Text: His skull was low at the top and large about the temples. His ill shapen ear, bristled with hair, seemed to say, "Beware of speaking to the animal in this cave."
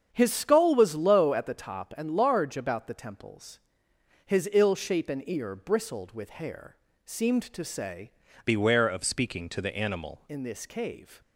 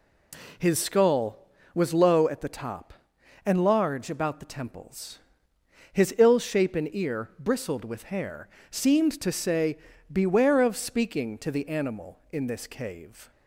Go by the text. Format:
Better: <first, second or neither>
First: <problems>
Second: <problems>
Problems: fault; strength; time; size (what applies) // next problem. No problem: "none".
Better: second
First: starts louder than the rest; strong; until 1.1 s; 7.5 dB // changes voice from "Beware" to "animal"; from 8.4 to 10.2 s; 1.8 s long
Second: none